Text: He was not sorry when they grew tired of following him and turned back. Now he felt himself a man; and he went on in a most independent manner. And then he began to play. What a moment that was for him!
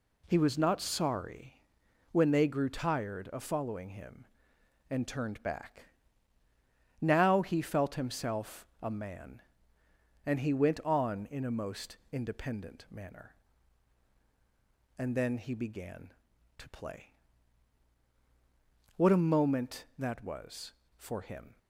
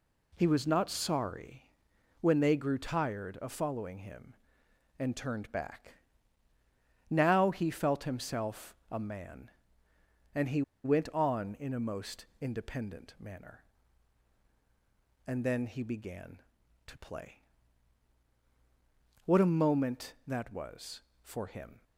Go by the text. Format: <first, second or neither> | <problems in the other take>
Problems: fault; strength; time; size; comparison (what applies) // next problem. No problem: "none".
first | pauses between "sorry" and "when"; noticeable; at 1.7 s; 0.48 s long; noticeable in the first // pauses between "himself" and "a"; slight; at 8.7 s; 0.16 s long; slight in the first // pauses between "he" and "went"; slight; at 10.6 s; 0.22 s long